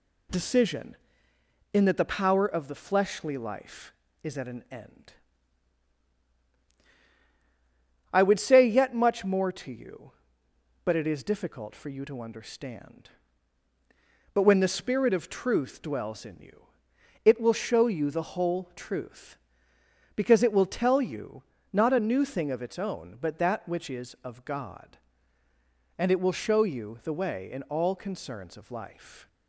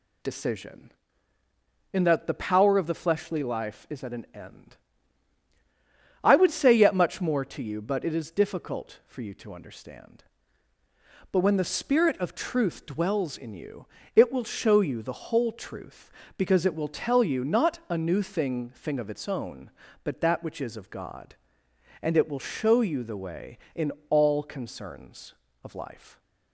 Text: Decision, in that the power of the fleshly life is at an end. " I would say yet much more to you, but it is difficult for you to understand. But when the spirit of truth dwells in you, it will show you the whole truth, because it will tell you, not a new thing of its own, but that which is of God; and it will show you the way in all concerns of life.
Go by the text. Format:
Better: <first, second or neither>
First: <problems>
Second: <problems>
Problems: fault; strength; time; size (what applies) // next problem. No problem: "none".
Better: first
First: none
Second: says "thing" twice; at 18.7 s // pauses between "in" and "all"; slight; at 23.9 s; 0.20 s long